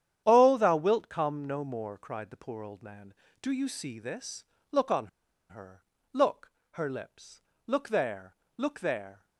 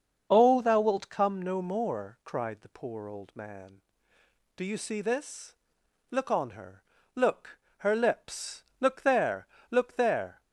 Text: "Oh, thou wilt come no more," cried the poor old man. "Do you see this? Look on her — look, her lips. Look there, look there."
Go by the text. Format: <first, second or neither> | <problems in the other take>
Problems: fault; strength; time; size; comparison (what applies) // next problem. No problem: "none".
second | starts louder than the rest; strong; until 1.2 s; 10 dB; also in the second // pauses between "on" and "her"; at 5.0 s; 0.42 s long